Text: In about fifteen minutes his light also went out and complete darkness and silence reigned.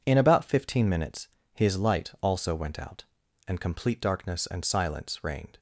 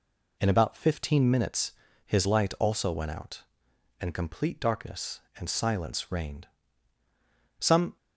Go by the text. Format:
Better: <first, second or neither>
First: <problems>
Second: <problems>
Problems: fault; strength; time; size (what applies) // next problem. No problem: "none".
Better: first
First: pauses between "minutes" and "his"; slight; at 1.2 s; 0.26 s long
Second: pauses between "minutes" and "his"; slight; at 1.7 s; 0.34 s long // goes on to say "Some"; slight; from 7.5 s on; 0.38 s long